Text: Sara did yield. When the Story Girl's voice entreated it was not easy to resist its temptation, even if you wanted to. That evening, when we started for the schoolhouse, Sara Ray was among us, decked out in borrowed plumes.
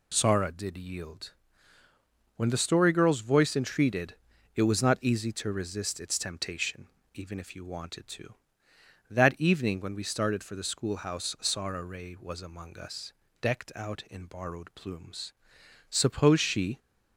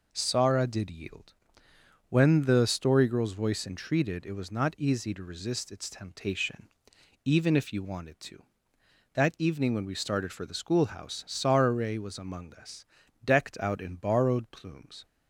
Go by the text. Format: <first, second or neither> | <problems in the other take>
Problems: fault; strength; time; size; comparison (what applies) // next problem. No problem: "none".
second | pauses between "entreated" and "it"; at 4.1 s; 0.40 s long // goes on to say "Suppose she"; noticeable; from 15.8 s on; 0.90 s long